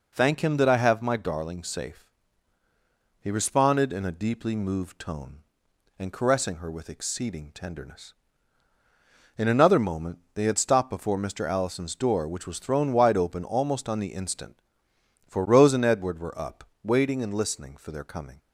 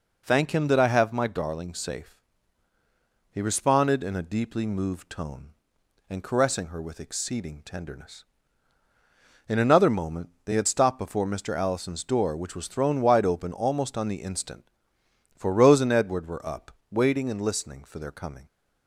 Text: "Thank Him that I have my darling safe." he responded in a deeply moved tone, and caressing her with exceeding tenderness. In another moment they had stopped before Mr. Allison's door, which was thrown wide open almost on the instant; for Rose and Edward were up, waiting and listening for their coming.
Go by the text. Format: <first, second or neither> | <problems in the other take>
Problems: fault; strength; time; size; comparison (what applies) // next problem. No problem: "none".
neither | pauses between "moment" and "they"; slight; the same in both